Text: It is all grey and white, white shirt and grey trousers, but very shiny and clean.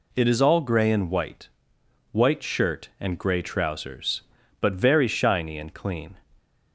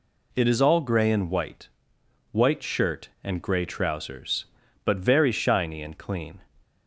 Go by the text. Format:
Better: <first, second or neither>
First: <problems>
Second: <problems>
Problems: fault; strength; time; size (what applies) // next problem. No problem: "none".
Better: neither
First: none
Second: none